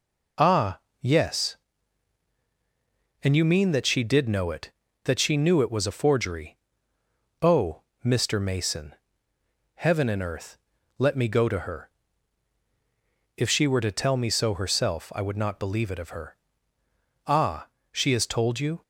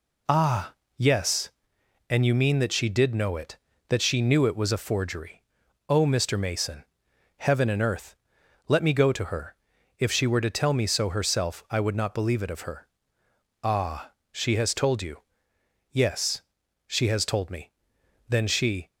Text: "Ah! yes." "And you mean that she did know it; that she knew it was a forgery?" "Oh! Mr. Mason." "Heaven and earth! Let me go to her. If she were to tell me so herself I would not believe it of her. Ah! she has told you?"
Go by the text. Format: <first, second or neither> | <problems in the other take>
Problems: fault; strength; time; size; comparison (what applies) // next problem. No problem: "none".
first | goes on to say "Yes she has told me Then she"; strong; from 15.9 s on; 2.9 s long